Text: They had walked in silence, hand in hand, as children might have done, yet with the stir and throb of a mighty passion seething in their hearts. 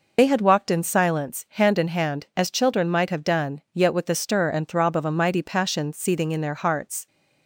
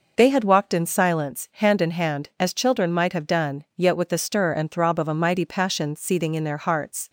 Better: second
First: loses the start of "They"; at 0.1 s; 40 ms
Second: none

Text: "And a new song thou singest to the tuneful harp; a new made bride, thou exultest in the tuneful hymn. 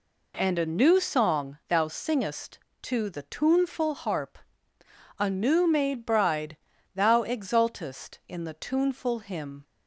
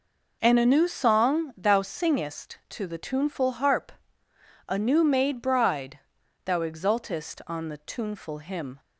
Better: first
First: none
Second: says "on" for "in"; at 7.4 s

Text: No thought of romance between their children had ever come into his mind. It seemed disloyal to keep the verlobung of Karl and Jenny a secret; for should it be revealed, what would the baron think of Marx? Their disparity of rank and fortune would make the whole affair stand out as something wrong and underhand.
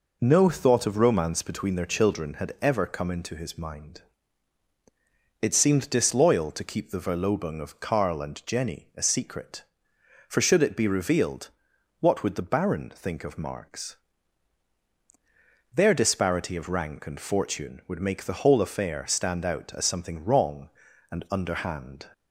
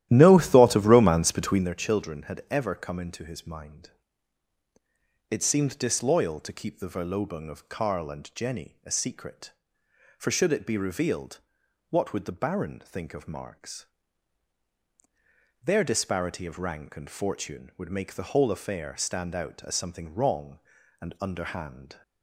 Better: first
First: none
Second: starts louder than the rest; strong; until 1.7 s; 13 dB

